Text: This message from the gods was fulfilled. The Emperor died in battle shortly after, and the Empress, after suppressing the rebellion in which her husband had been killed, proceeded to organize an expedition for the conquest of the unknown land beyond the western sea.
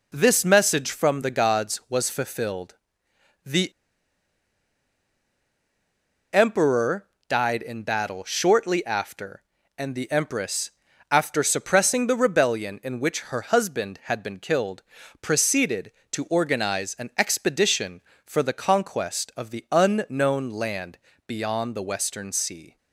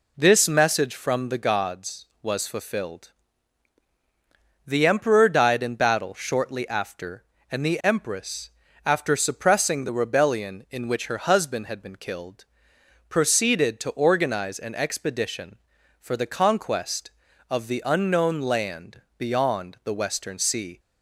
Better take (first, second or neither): second